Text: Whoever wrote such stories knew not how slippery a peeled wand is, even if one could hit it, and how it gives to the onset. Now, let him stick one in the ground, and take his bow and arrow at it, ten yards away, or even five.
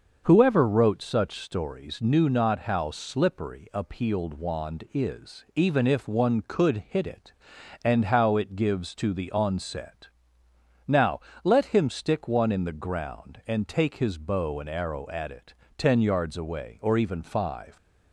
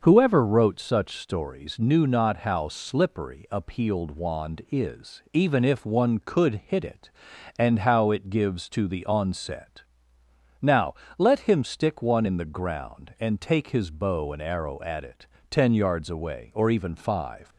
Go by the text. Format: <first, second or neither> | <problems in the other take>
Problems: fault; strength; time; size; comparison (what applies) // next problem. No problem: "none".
neither | starts louder than the rest; the same in both